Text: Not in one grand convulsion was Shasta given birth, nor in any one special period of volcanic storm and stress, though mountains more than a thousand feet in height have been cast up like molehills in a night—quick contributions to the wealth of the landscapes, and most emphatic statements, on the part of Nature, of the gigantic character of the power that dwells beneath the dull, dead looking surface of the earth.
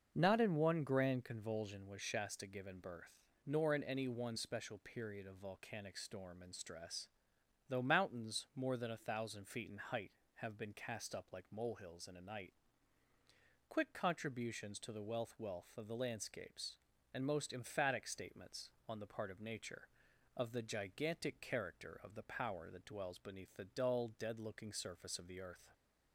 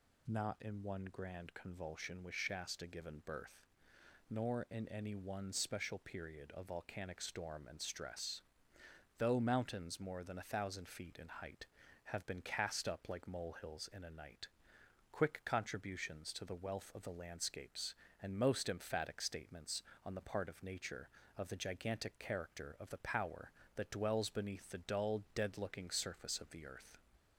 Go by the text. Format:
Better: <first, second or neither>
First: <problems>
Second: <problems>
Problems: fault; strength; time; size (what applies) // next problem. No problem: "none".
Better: second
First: starts louder than the rest; until 1.1 s; 6.5 dB // says "wealth" twice; at 15.3 s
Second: none